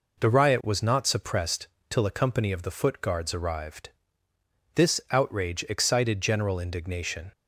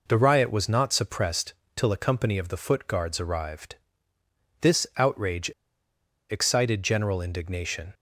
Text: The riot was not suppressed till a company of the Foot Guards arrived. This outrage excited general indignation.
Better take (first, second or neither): first